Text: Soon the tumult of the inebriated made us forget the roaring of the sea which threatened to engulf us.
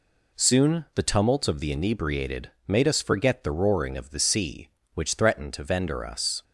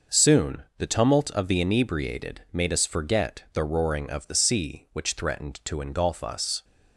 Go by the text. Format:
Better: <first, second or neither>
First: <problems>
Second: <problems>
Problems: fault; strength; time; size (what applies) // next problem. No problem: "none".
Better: second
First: pauses between "inebriated" and "made"; slight; at 2.4 s; 0.18 s long // says "vendor" for "engulf"; at 5.6 s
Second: none